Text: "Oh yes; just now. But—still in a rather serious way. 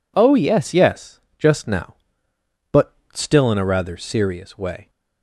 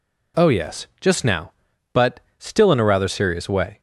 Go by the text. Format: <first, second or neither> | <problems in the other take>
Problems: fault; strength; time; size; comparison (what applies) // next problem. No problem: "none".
second | says "yes" twice; at 0.7 s